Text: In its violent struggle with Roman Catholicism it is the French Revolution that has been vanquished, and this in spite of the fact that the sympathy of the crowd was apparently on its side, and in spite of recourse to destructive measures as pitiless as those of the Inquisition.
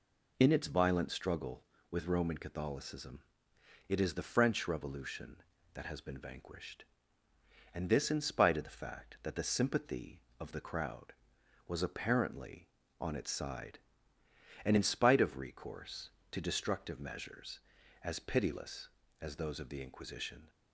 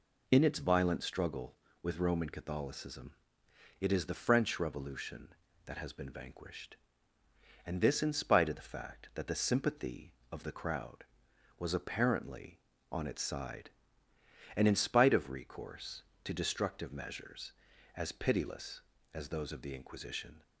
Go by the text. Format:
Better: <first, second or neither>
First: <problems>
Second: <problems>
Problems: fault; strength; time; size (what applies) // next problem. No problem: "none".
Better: neither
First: pauses between "Catholicism" and "it"; noticeable; at 3.2 s; 0.64 s long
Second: pauses between "Catholicism" and "it"; noticeable; at 3.1 s; 0.64 s long